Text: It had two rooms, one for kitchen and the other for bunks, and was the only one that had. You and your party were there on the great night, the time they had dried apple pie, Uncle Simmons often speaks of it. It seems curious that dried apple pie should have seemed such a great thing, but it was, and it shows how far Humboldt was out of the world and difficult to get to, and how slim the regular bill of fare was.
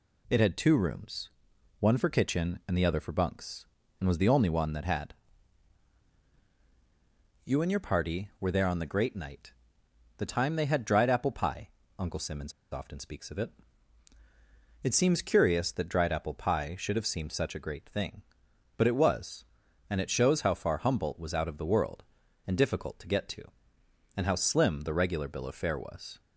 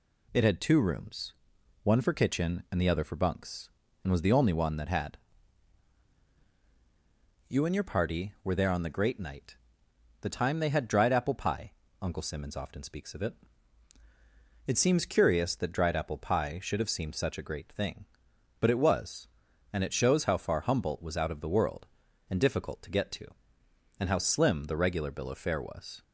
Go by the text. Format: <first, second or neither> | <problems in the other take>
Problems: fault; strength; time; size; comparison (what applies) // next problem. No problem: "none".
second | pauses between "Simmons" and "often"; slight; at 12.5 s; 0.19 s long